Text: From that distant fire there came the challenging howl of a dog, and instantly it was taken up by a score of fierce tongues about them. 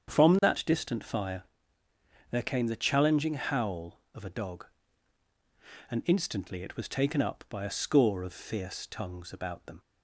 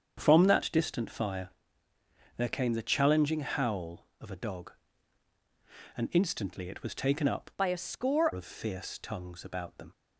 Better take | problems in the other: first | starts louder than the rest; strong; until 1.2 s; 7.5 dB; strong in the first // pauses between "fire" and "there"; noticeable; at 1.4 s; 0.90 s long; noticeable in the first // changes voice from "by" to "score"; from 7.5 to 8.3 s; 0.8 s long

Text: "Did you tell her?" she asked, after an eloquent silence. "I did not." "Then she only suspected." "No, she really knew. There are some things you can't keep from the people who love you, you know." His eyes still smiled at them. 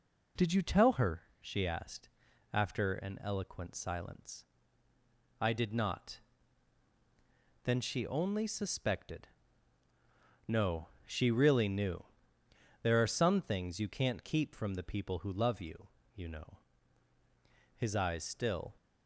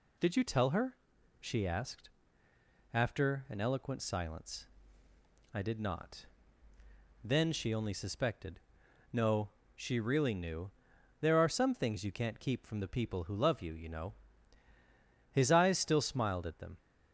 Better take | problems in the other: second | stops before "smiled at them"; at 18.7 s

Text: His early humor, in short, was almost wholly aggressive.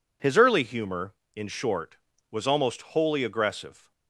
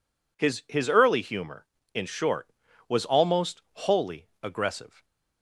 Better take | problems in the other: first | says "His" twice; at 0.6 s // pauses between "wholly" and "aggressive"; slight; at 4.2 s; 0.16 s long // stays silent after the last word; slight; from 4.8 s on; 0.6 s long

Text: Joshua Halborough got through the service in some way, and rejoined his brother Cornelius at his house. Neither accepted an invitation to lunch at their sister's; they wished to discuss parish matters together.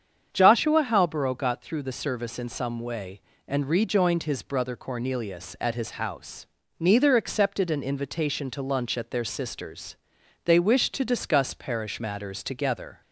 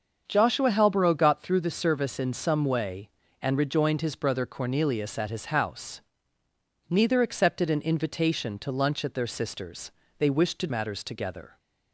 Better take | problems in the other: first | starts louder than the rest; until 1.2 s; 6.5 dB; strong in the first // skips "discuss parish"; at 10.6 s

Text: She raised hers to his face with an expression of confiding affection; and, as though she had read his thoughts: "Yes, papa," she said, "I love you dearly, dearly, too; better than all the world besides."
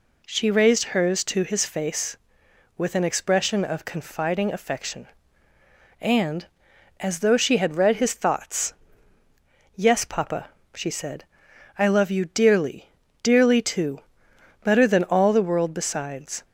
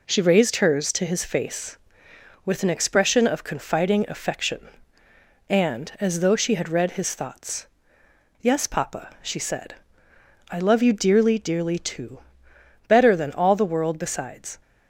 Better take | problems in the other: neither | none

